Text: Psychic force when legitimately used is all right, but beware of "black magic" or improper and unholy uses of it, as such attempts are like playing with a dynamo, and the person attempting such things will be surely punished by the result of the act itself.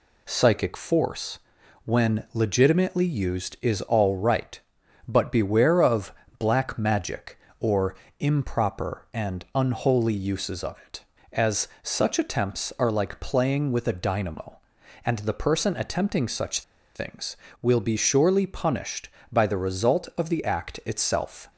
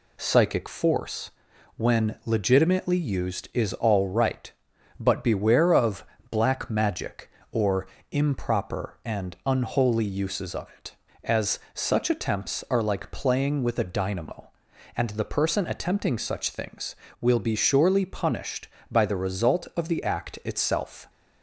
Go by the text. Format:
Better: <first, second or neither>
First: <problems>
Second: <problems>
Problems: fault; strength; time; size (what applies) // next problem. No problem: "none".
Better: second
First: pauses between "force" and "when"; noticeable; at 1.3 s; 0.48 s long // pauses between "of" and "black"; slight; at 6.1 s; 0.26 s long // pauses between "or" and "improper"; slight; at 7.9 s; 0.26 s long // pauses between "as" and "such"; slight; at 11.6 s; 0.16 s long // pauses between "such" and "things"; slight; at 16.6 s; 0.34 s long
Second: pauses between "force" and "when"; noticeable; at 1.2 s; 0.48 s long // pauses between "of" and "black"; slight; at 6.0 s; 0.26 s long // pauses between "or" and "improper"; slight; at 7.8 s; 0.26 s long // pauses between "as" and "such"; slight; at 11.5 s; 0.16 s long